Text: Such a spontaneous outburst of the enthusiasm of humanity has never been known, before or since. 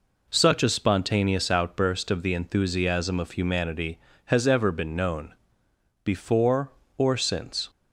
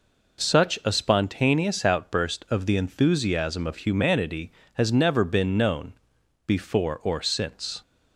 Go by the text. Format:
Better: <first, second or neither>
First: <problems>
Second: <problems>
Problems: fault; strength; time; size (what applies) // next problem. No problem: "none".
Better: second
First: says "ever" for "never"; at 4.4 s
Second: none